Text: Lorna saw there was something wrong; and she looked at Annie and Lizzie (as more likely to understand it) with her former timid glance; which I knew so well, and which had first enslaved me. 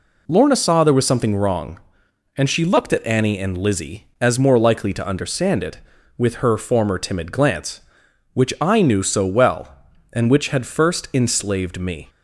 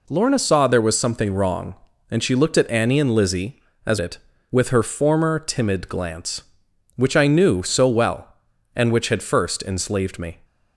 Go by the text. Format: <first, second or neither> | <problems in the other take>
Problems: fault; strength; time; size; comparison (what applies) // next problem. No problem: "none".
first | skips "more likely to understand"; at 3.9 s